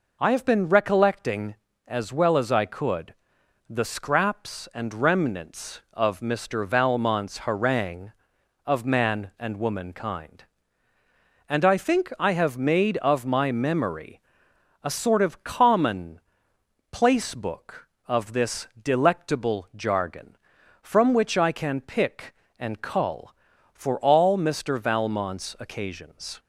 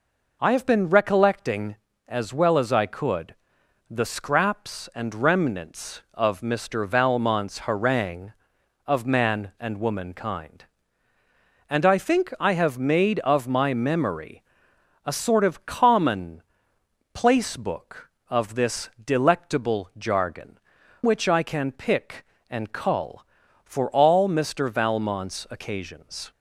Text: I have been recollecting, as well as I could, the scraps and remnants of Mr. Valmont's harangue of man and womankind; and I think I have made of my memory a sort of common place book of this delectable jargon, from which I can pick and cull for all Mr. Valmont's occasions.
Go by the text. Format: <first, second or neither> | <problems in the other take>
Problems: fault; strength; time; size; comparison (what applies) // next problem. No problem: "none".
first | pauses between "memory" and "a"; noticeable; at 14.4 s; 0.64 s long; noticeable in the first // pauses between "common" and "place"; noticeable; at 16.4 s; 0.72 s long; noticeable in the first // skips "from"; at 20.8 s